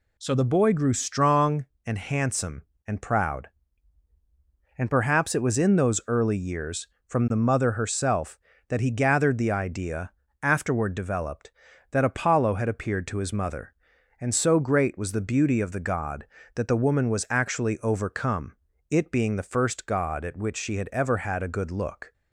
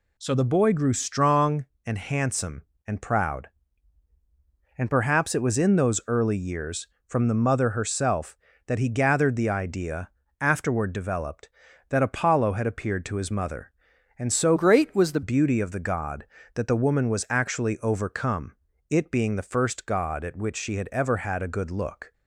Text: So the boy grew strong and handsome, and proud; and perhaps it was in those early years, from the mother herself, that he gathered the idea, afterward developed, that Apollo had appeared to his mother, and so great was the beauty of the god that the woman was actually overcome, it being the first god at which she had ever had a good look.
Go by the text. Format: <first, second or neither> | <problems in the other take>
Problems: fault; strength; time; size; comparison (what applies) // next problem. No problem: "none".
first | changes voice from "great" to "the"; from 14.5 to 15.2 s; 0.7 s long